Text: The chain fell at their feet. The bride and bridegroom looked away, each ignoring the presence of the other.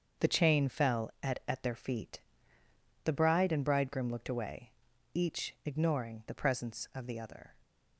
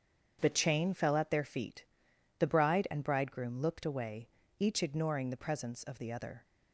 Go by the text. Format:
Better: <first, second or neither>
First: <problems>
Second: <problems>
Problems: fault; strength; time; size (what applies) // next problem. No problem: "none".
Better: second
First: starts louder than the rest; until 1.3 s; 7 dB // says "at" twice; at 1.4 s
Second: starts louder than the rest; strong; until 1.4 s; 7.5 dB